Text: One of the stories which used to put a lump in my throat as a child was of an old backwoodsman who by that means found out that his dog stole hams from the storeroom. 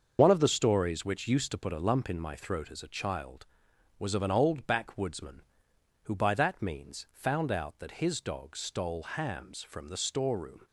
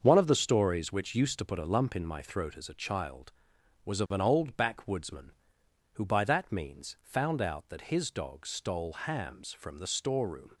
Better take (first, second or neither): second